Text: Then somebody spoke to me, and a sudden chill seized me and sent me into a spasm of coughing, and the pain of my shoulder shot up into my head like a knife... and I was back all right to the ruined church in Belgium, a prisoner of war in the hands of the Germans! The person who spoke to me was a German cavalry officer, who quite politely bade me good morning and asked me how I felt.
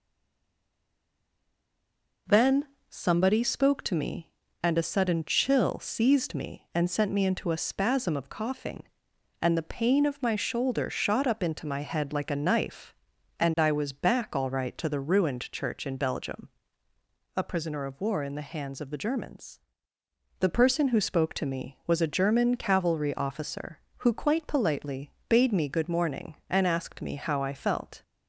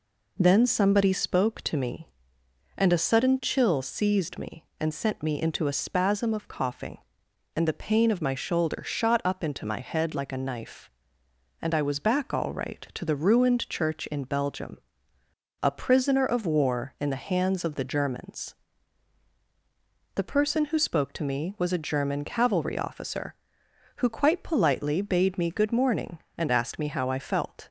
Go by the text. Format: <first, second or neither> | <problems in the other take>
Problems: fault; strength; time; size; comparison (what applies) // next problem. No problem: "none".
second | stays silent before the first word; until 2.2 s; 2.2 s long // pauses between "Then" and "somebody"; slight; at 2.6 s; 0.24 s long // pauses between "politely" and "bade"; slight; at 25.1 s; 0.18 s long